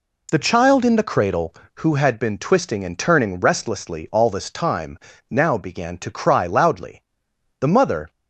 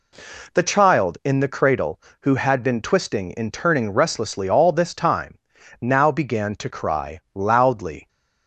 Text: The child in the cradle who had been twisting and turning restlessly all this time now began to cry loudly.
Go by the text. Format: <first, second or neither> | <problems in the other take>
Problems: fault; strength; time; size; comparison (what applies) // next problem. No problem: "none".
second | pauses between "time" and "now"; slight; at 4.9 s; 0.32 s long; also in the second // goes on to say "The mother"; from 7.5 s on; 0.52 s long